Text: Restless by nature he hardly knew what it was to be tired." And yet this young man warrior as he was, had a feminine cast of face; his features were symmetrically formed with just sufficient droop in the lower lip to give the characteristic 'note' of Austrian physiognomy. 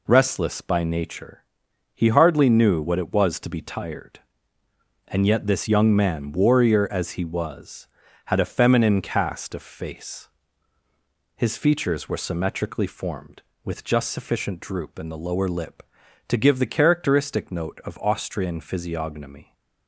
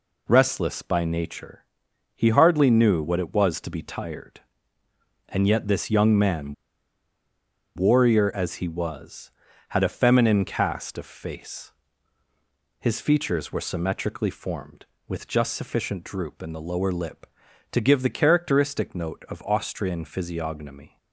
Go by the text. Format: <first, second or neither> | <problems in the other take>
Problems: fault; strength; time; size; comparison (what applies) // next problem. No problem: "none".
first | pauses between "nature" and "he"; noticeable; at 1.6 s; 0.56 s long; noticeable in the first // pauses between "man" and "warrior"; at 6.5 s; 1.2 s long